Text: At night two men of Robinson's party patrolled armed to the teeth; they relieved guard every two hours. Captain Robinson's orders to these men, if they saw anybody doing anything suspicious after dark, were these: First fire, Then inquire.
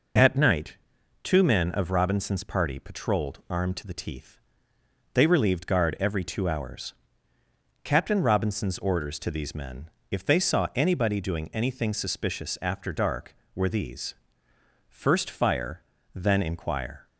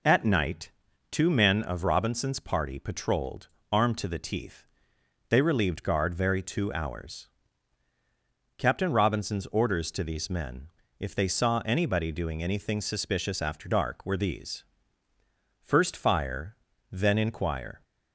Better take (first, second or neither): first